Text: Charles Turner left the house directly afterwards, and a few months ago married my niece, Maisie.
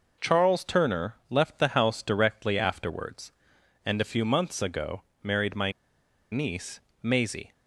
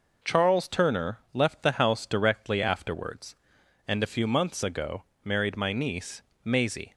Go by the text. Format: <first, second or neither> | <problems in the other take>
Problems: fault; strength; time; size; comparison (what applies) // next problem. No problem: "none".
second | pauses between "ago" and "married"; slight; at 5.0 s; 0.20 s long; slight in the second // pauses between "my" and "niece"; noticeable; at 5.7 s; 0.59 s long